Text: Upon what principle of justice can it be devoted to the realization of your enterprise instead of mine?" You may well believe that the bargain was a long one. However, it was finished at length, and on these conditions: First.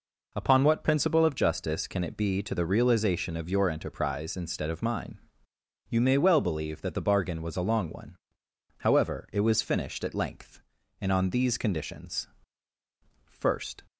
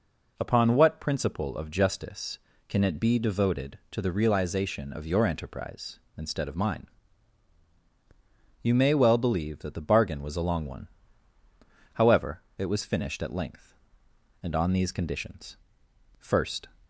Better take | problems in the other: second | skips "devoted"; at 2.4 s

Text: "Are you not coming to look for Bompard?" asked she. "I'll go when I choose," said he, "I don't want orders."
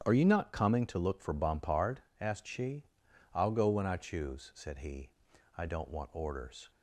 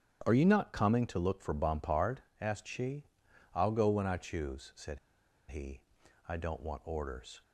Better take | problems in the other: first | starts louder than the rest; strong; until 1.2 s; 9.5 dB; strong in the first // pauses between "said" and "he"; noticeable; at 4.9 s; 0.51 s long

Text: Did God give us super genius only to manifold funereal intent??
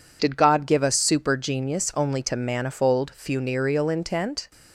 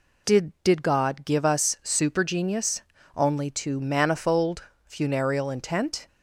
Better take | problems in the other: first | says "Did" twice; at 0.6 s // pauses between "genius" and "only"; slight; at 2.8 s; 0.34 s long // pauses between "manifold" and "funereal"; slight; at 4.6 s; 0.20 s long

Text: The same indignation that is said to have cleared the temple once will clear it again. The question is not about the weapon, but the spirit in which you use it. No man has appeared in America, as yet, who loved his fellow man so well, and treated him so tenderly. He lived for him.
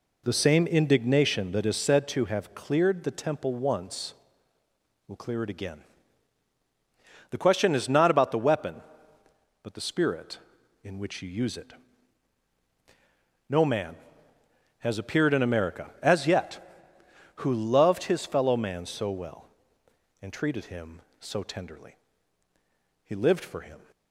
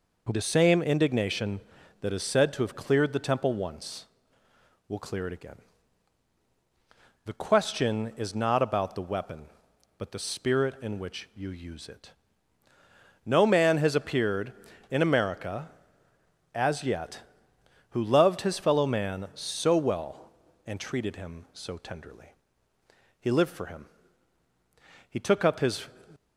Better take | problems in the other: first | goes on to say "He took up his"; noticeable; from 25.0 s on; 0.78 s long

